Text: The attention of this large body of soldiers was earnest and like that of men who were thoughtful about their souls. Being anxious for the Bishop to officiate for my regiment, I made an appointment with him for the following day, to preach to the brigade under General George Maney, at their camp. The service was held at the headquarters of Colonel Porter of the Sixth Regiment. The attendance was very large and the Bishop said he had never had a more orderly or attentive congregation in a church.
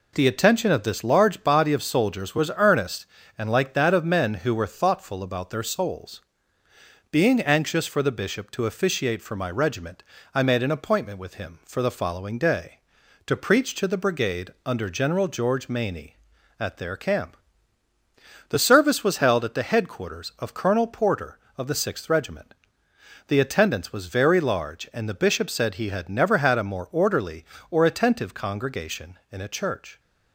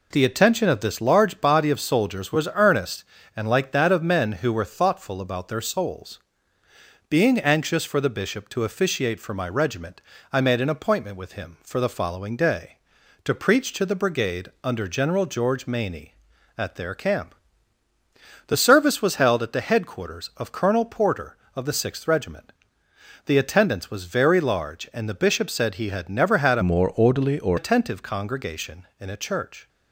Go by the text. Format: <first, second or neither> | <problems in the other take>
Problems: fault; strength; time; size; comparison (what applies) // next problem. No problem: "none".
first | pauses between "brigade" and "under"; slight; at 14.4 s; 0.16 s long; slight in the first // changes voice from "more" to "or"; from 26.6 to 27.5 s; 0.9 s long